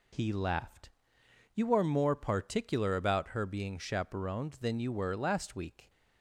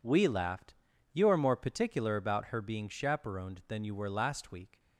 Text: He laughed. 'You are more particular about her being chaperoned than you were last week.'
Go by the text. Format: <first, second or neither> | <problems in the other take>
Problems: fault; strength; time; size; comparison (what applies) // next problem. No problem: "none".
first | says "We" for "He"; at 0.0 s